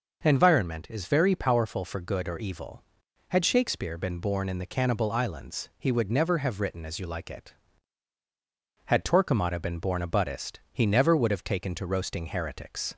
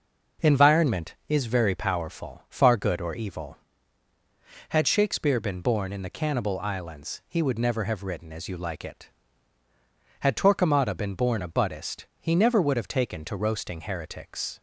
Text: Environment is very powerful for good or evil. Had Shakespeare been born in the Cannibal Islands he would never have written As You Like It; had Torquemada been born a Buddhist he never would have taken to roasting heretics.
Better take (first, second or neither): first